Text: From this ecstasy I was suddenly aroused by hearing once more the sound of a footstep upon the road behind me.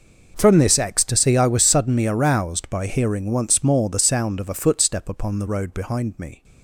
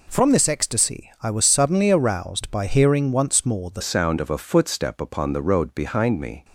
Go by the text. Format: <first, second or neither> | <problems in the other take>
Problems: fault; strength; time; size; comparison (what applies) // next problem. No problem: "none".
first | changes voice at "sound"; from 3.8 s on; 2.6 s long